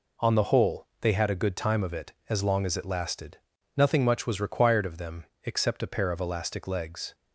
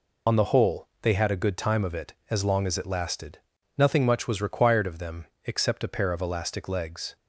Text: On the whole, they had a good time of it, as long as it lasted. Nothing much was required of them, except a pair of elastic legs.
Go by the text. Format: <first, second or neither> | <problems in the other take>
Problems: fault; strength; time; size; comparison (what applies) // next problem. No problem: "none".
first | loses the start of "On"; at 0.2 s; 65 ms